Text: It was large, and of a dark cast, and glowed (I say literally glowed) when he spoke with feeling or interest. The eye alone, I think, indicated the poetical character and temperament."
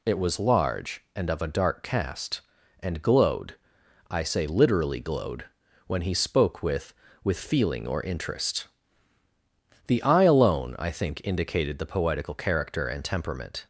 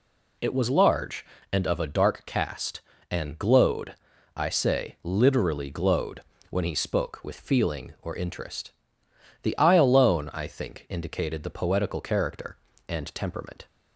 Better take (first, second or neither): second